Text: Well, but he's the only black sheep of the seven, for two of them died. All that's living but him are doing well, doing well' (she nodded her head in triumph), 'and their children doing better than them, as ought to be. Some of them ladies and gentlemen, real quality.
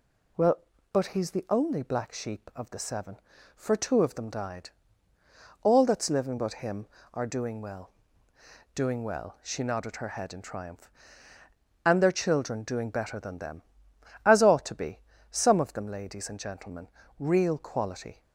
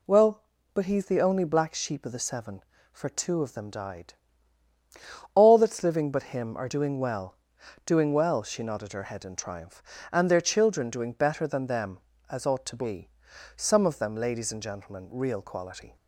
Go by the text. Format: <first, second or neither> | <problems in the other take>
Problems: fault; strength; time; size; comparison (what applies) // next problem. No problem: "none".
neither | none